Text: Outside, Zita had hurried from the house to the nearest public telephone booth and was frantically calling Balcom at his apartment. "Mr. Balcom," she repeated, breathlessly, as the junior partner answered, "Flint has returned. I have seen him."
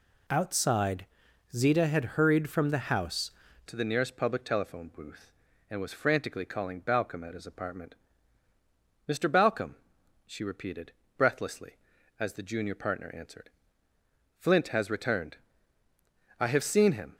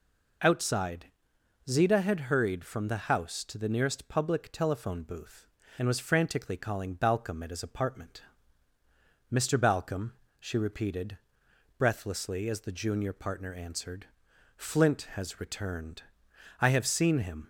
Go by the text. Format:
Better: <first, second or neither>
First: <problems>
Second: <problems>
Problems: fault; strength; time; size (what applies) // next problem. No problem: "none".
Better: second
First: changes voice at "to"; from 3.6 s on; 13.5 s long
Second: none